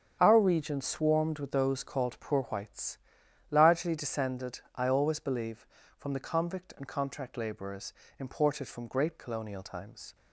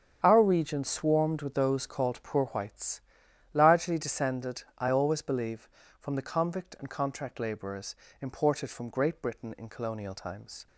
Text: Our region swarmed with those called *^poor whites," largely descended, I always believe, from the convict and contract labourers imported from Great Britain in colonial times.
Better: second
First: starts louder than the rest; strong; until 1.2 s; 8 dB // pauses between "labourers" and "imported"; slight; at 7.9 s; 0.28 s long // skips "Britain in"; at 9.1 s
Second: starts louder than the rest; strong; until 1.2 s; 8 dB // pauses between "labourers" and "imported"; slight; at 7.9 s; 0.28 s long

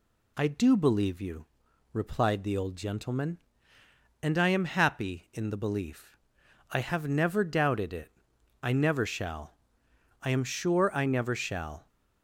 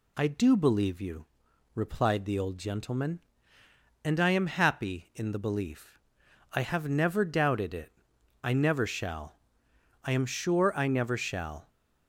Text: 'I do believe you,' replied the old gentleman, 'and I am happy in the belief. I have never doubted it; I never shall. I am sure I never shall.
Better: neither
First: none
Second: none

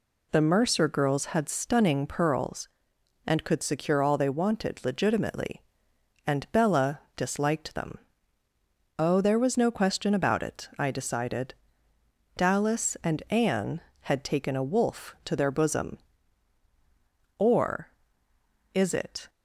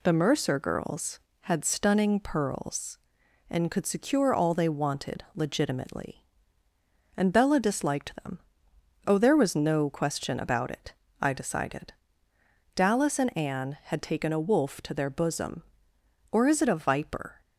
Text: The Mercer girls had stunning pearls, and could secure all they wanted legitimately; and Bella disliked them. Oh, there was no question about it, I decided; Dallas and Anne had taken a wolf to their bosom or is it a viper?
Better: second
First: pauses between "Bella" and "disliked"; slight; at 7.0 s; 0.16 s long // stops before "a viper"; at 19.2 s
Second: none

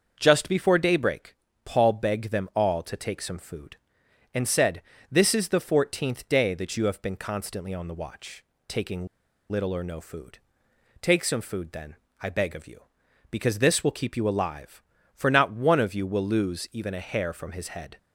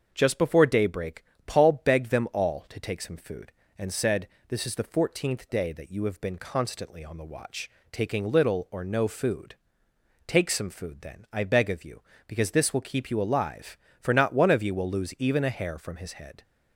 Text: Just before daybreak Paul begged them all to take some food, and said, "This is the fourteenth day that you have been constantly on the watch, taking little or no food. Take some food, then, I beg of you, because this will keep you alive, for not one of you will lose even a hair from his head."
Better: second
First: starts louder than the rest; until 1.2 s; 6.5 dB // pauses between "daybreak" and "Paul"; slight; at 1.3 s; 0.30 s long // pauses between "taking" and "little"; at 9.0 s; 0.44 s long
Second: starts louder than the rest; until 1.1 s; 6.5 dB // pauses between "daybreak" and "Paul"; slight; at 1.2 s; 0.22 s long

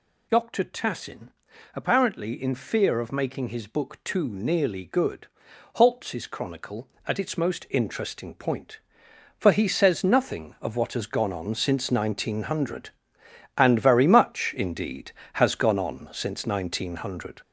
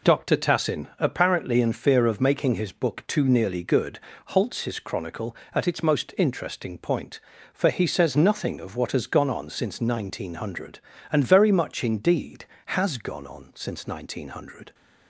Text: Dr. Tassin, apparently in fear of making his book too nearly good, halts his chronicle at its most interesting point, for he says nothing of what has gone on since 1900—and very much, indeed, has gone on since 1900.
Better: second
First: gets louder; noticeable; throughout; 5.5 dB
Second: none

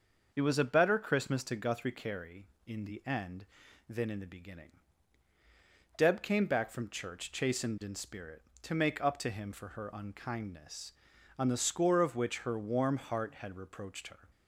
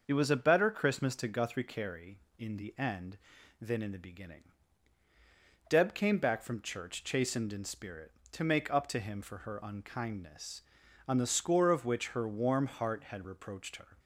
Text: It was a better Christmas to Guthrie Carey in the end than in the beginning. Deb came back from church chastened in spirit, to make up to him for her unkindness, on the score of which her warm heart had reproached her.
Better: neither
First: starts louder than the rest; until 1.3 s; 6.5 dB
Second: starts louder than the rest; until 1.0 s; 6.5 dB

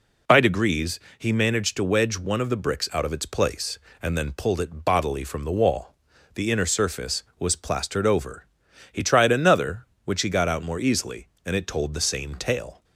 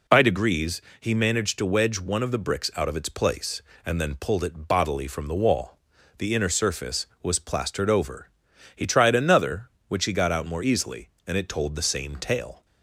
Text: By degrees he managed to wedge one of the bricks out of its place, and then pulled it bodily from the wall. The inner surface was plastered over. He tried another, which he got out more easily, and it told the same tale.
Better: neither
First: pauses between "degrees" and "he"; slight; at 0.9 s; 0.20 s long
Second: pauses between "degrees" and "he"; slight; at 0.8 s; 0.20 s long

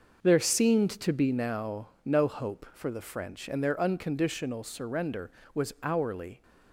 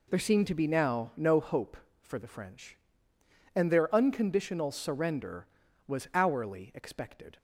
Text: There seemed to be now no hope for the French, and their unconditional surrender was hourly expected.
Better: second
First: pauses between "now" and "no"; slight; at 1.8 s; 0.16 s long // stops before "expected"; at 6.4 s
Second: none

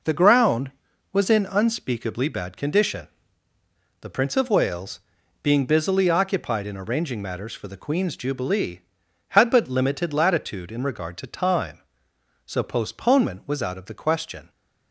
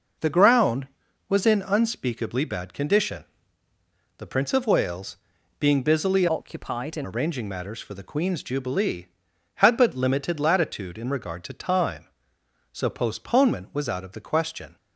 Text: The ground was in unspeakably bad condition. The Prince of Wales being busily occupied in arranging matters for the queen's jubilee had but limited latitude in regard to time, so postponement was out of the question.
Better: first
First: pauses between "Wales" and "being"; at 5.0 s; 0.42 s long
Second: pauses between "Wales" and "being"; at 5.1 s; 0.42 s long // changes voice from "occupied" to "in"; from 6.2 to 7.0 s; 0.8 s long

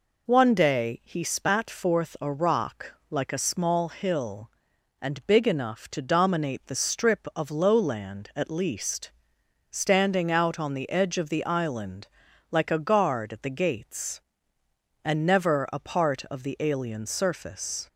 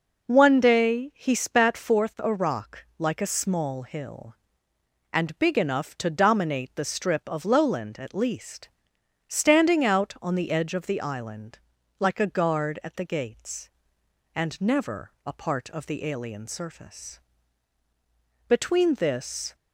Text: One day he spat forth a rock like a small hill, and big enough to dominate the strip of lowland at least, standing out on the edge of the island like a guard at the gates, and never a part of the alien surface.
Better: first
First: pauses between "rock" and "like"; slight; at 2.9 s; 0.16 s long // pauses between "island" and "like"; at 12.0 s; 0.42 s long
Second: pauses between "rock" and "like"; slight; at 2.8 s; 0.16 s long // pauses between "island" and "like"; at 11.5 s; 0.42 s long // goes on to say "Between this"; noticeable; from 18.4 s on; 1.0 s long

